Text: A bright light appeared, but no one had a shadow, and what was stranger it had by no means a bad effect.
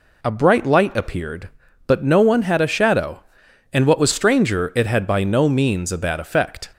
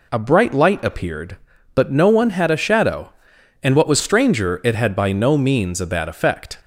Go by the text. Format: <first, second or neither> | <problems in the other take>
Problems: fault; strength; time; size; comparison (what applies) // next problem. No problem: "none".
neither | none